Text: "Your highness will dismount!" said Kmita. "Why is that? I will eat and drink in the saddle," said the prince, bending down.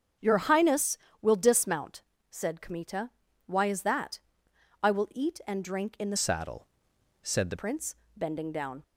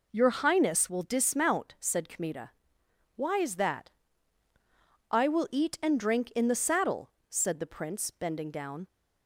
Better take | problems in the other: second | starts louder than the rest; strong; until 1.4 s; 7.5 dB // changes voice from "saddle" to "the"; from 6.1 to 7.5 s; 1.4 s long

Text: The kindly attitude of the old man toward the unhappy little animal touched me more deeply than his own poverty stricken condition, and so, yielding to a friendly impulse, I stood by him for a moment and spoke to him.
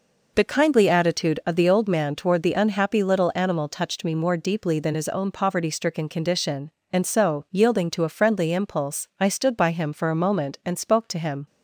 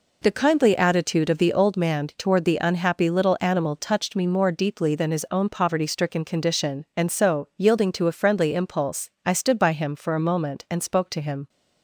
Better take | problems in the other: neither | none

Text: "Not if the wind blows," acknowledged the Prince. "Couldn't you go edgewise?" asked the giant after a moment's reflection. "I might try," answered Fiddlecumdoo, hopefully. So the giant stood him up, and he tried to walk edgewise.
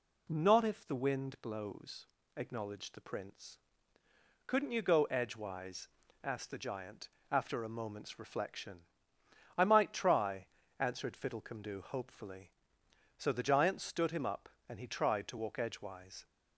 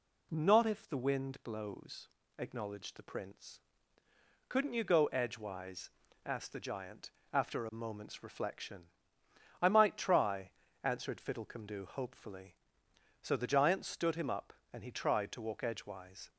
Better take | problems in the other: neither | pauses between "giant" and "after"; slight; the same in both

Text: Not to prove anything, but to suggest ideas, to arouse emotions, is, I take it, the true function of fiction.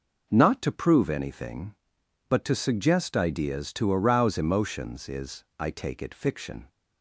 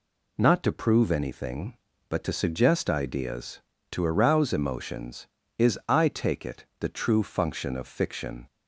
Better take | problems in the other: second | skips "the true function of"; at 6.1 s

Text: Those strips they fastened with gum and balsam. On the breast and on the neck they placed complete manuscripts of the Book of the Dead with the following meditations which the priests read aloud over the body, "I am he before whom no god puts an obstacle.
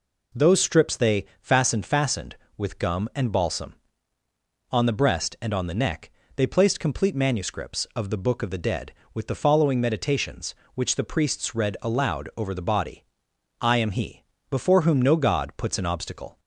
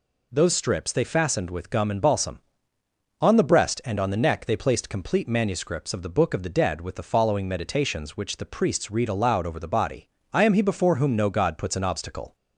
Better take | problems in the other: second | says "fastened" twice; at 1.8 s // pauses between "neck" and "they"; slight; at 6.0 s; 0.26 s long // pauses between "he" and "before"; slight; at 14.2 s; 0.26 s long

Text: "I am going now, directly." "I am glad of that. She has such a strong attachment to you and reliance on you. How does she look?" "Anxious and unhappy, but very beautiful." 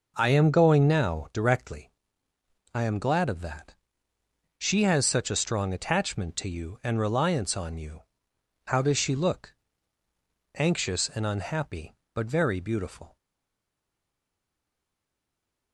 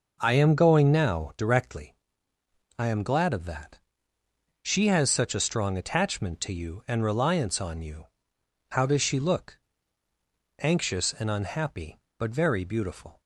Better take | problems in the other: second | stays silent after the last word; strong; from 13.1 s on; 2.6 s long

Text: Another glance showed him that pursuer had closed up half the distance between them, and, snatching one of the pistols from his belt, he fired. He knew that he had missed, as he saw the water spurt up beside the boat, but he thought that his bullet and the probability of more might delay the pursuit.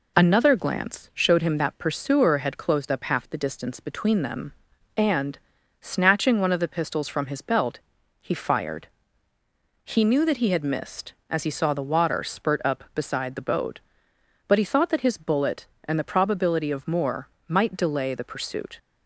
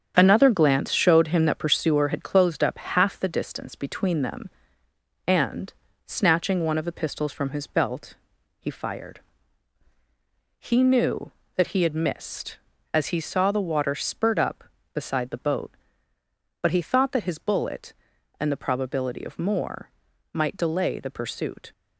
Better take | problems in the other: first | gets quieter; throughout; 6.5 dB // pauses between "more" and "might"; at 19.8 s; 0.44 s long; slight in the first

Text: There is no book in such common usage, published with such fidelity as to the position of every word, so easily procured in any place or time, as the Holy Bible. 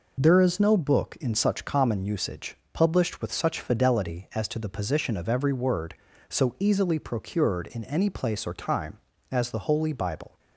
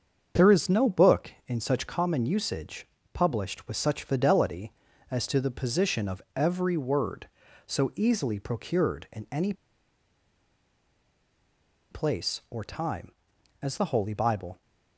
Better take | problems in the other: first | starts louder than the rest; until 1.5 s; 7 dB // pauses between "of" and "every"; slight; at 6.2 s; 0.16 s long // pauses between "any" and "place"; strong; at 9.5 s; 2.3 s long

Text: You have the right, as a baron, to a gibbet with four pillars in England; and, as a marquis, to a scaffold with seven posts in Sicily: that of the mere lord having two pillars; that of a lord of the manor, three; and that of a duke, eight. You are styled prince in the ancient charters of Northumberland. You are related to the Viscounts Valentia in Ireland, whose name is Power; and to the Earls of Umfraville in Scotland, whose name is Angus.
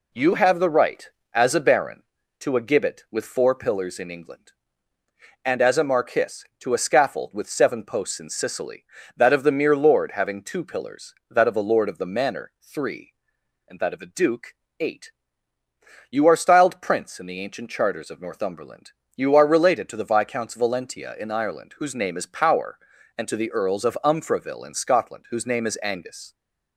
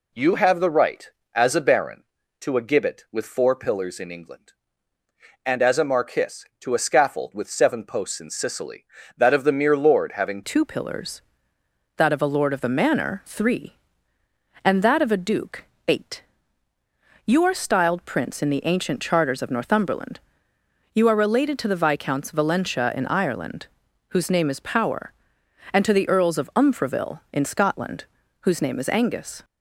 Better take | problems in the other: first | changes voice at "two"; from 10.4 s on; 19.0 s long

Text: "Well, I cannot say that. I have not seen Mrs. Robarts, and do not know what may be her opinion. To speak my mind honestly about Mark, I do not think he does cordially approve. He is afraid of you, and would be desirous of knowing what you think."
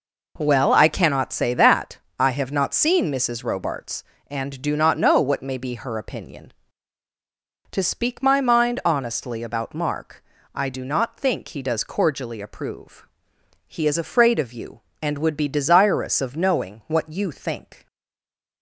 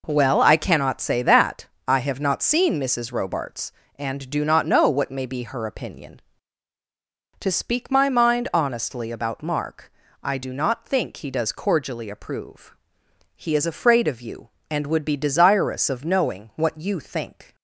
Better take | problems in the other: second | stays silent after the last word; slight; from 17.8 s on; 0.8 s long

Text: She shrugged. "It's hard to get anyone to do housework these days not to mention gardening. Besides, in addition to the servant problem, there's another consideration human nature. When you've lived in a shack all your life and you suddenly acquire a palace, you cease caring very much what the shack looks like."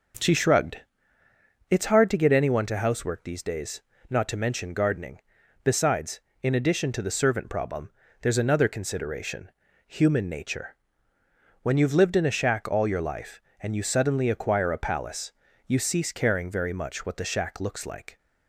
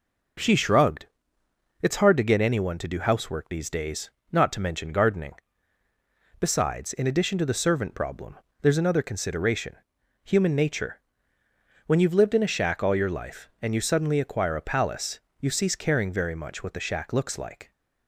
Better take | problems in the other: second | starts louder than the rest; noticeable; until 2.1 s; 6 dB // skips "do"; at 2.7 s // pauses between "days" and "not"; slight; at 3.8 s; 0.28 s long; slight in the second // pauses between "consideration" and "human"; at 9.4 s; 0.38 s long; noticeable in the second

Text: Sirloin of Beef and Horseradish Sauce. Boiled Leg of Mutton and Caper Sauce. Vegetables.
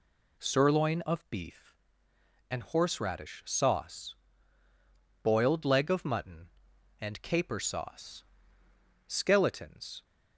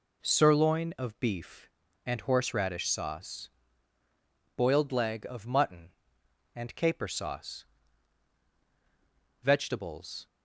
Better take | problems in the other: second | says "Skeletons" for "Vegetables"; at 9.0 s

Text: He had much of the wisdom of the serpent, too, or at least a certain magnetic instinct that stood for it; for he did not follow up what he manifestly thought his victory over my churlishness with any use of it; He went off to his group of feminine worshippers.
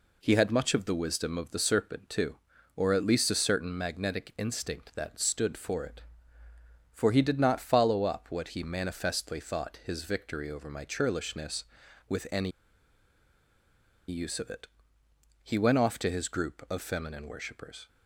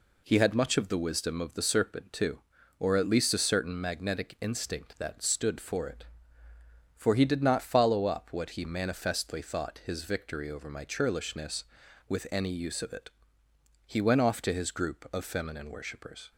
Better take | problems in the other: second | pauses between "any" and "use"; strong; at 12.5 s; 1.5 s long

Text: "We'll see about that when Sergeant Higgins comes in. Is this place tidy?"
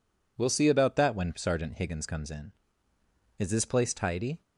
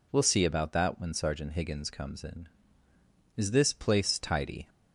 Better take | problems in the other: neither | none

